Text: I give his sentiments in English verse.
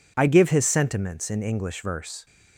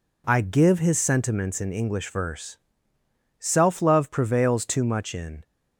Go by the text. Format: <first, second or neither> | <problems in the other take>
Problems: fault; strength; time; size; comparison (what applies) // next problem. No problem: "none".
first | goes on to say "Self love prevails too much in"; strong; from 3.3 s on; 2.0 s long